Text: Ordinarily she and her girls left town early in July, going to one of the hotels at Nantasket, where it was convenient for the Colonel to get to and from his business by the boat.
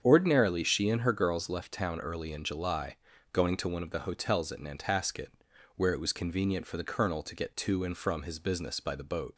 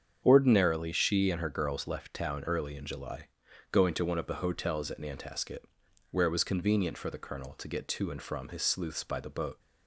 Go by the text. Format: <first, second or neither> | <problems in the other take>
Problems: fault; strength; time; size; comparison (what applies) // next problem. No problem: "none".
first | starts louder than the rest; strong; until 1.2 s; 7.5 dB; strong in the first // says "sleuths" for "business"; at 8.6 s